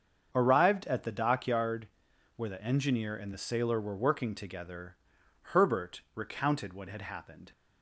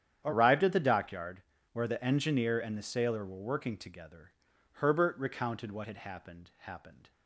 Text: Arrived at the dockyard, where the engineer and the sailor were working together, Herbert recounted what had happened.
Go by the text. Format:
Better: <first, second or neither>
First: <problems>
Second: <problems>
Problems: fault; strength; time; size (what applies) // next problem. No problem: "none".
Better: first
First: starts louder than the rest; until 1.3 s; 7 dB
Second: starts louder than the rest; strong; until 1.2 s; 9.5 dB // says "happened" twice; at 6.5 s